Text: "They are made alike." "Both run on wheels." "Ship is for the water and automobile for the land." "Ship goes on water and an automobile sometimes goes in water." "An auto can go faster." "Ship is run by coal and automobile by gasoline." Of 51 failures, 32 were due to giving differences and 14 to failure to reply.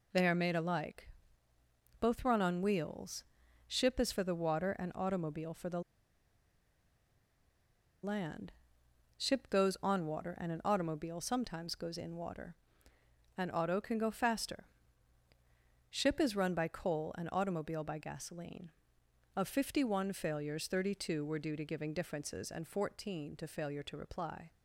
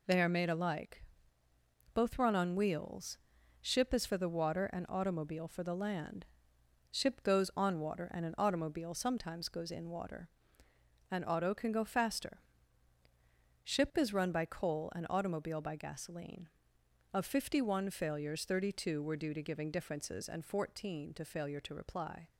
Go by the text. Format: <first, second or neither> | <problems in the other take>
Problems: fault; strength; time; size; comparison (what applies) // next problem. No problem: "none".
second | pauses between "the" and "land"; strong; at 5.8 s; 2.2 s long